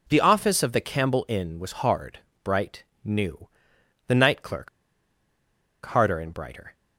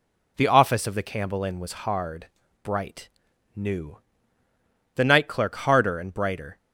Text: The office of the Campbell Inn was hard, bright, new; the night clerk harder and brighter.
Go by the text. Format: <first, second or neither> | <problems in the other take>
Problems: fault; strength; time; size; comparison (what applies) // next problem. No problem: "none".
second | pauses between "clerk" and "harder"; at 4.6 s; 1.1 s long